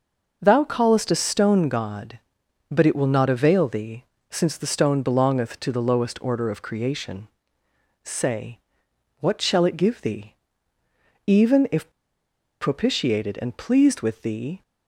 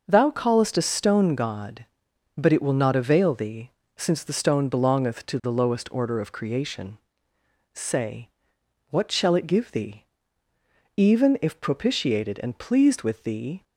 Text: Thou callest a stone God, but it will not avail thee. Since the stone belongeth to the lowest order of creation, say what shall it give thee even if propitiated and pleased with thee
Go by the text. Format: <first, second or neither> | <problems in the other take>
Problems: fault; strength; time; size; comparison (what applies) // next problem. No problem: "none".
second | pauses between "say" and "what"; noticeable; at 8.5 s; 0.62 s long; noticeable in the second // pauses between "thee" and "even"; noticeable; at 10.3 s; 0.92 s long; noticeable in the second // pauses between "if" and "propitiated"; noticeable; at 11.8 s; 0.71 s long